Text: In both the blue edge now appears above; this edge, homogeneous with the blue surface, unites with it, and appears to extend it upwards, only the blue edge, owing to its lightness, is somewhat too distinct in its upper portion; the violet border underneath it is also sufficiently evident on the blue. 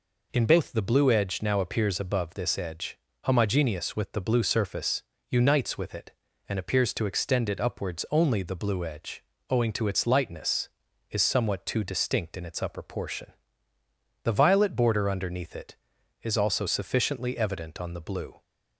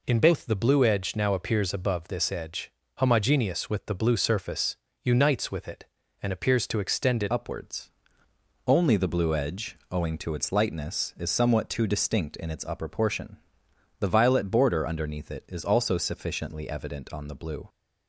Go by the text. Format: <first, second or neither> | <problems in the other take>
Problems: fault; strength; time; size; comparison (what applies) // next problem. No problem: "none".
first | changes voice at "upwards"; from 7.2 s on; 10.4 s long